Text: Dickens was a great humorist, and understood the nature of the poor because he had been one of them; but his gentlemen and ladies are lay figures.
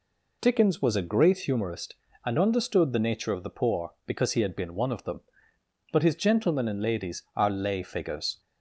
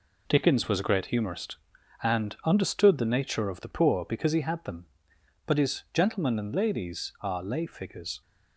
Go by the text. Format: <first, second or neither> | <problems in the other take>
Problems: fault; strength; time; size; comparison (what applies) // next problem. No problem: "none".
first | skips "been one of"; at 4.6 s